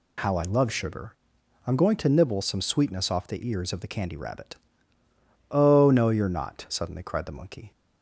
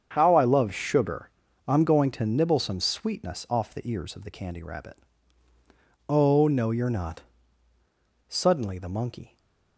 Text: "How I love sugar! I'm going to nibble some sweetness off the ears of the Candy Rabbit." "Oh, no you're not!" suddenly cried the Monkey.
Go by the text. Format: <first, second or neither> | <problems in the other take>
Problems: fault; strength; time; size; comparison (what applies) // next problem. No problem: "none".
first | starts louder than the rest; strong; until 1.1 s; 7.5 dB // skips "cried"; at 8.7 s // stays silent after the last word; slight; from 9.2 s on; 0.5 s long